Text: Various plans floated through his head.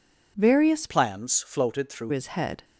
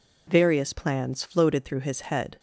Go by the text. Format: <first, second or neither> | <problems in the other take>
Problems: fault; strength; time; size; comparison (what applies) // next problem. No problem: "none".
second | changes voice from "plans" to "through"; from 0.8 to 2.1 s; 1.3 s long